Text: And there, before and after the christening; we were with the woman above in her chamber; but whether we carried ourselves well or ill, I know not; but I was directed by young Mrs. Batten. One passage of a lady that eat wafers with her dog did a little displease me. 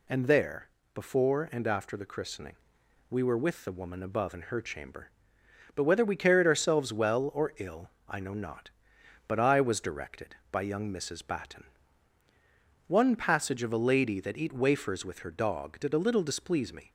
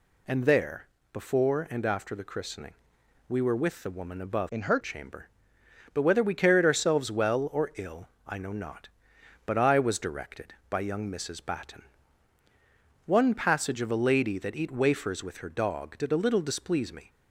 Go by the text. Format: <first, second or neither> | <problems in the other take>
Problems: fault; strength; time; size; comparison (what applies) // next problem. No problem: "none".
first | changes voice from "in" to "her"; from 4.4 to 4.7 s; 0.3 s long